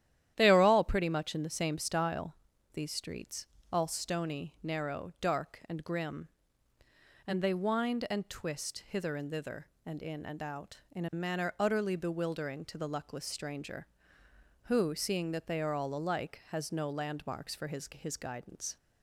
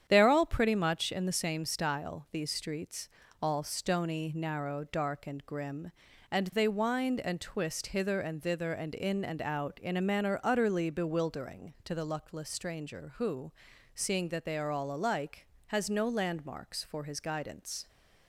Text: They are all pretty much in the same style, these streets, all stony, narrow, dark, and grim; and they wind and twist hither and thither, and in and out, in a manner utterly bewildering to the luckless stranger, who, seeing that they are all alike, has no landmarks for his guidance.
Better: second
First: starts louder than the rest; strong; until 1.3 s; 11.5 dB // says "his" twice; at 17.9 s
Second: starts louder than the rest; strong; until 1.0 s; 9 dB

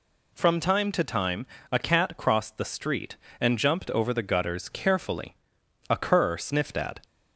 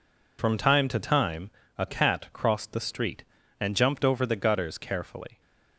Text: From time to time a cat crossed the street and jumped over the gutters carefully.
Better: second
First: pauses between "time" and "a"; slight; at 1.4 s; 0.26 s long // goes on to say "A cur sniffed at"; noticeable; from 5.9 s on; 1.1 s long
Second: pauses between "time" and "a"; slight; at 1.4 s; 0.26 s long

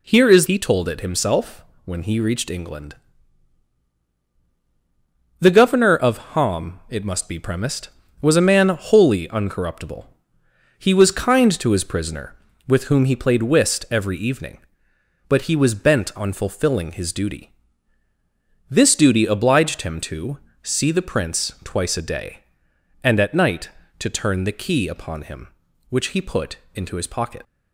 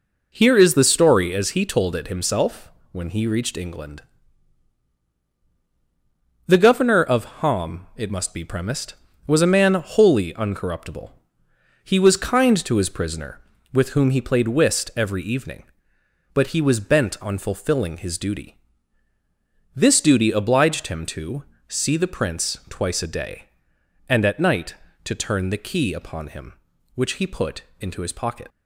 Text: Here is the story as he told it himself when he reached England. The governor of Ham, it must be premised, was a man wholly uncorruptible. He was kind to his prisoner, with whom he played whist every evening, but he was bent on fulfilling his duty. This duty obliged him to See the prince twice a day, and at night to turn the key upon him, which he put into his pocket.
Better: second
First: skips "the story as"; at 0.4 s // pauses between "himself" and "when"; slight; at 1.6 s; 0.20 s long // pauses between "to" and "See"; slight; at 20.3 s; 0.24 s long // pauses between "put" and "into"; slight; at 26.5 s; 0.16 s long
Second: pauses between "himself" and "when"; slight; at 2.7 s; 0.20 s long // pauses between "to" and "See"; slight; at 21.4 s; 0.24 s long // pauses between "put" and "into"; slight; at 27.6 s; 0.16 s long

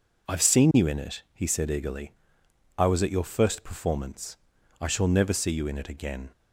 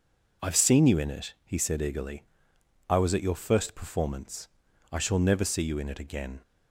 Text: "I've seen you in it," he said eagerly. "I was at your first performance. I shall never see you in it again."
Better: neither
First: none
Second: none

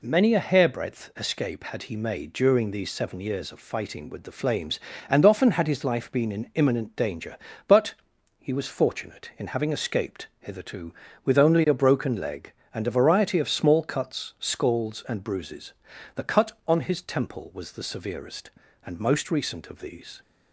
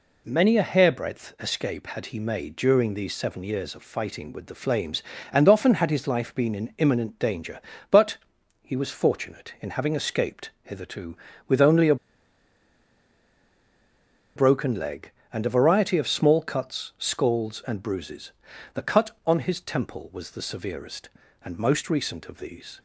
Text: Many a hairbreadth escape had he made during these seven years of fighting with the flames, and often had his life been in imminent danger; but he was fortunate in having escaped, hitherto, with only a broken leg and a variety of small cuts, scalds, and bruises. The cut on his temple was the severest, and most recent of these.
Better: first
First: pauses between "but" and "he"; noticeable; at 7.9 s; 0.46 s long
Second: pauses between "but" and "he"; noticeable; at 8.1 s; 0.46 s long // pauses between "a" and "broken"; strong; at 11.9 s; 2.4 s long

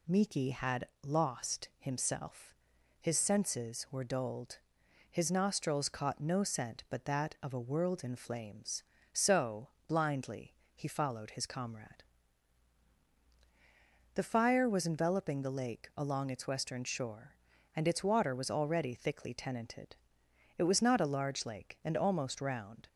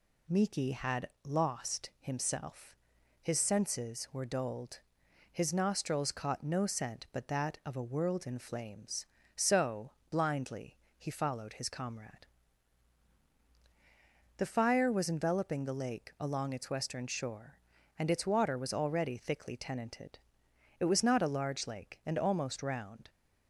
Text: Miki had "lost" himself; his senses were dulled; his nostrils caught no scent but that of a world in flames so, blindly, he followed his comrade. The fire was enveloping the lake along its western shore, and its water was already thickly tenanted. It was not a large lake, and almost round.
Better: neither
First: pauses between "had" and "lost"; slight; at 0.8 s; 0.18 s long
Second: pauses between "had" and "lost"; slight; at 1.0 s; 0.18 s long

